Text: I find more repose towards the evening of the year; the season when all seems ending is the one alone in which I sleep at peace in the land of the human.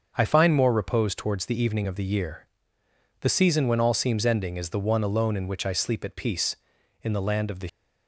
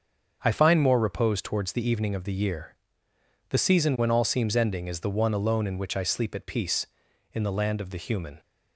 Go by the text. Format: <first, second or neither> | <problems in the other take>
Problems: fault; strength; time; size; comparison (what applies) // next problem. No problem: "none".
second | starts louder than the rest; until 1.1 s; 6.5 dB; also in the second // stops before "human"; at 7.6 s